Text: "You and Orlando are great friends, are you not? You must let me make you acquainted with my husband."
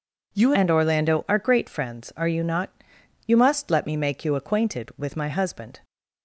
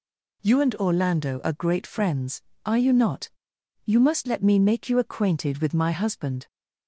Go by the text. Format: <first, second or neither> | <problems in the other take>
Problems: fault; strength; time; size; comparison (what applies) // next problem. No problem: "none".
second | changes voice at "and"; from 0.5 s on; 5.2 s long